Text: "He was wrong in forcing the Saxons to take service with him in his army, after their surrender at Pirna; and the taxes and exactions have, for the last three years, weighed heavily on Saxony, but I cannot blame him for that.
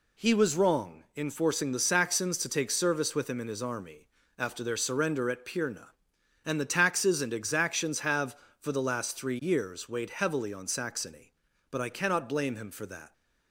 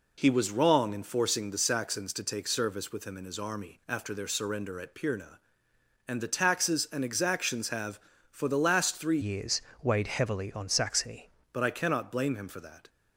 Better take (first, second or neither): first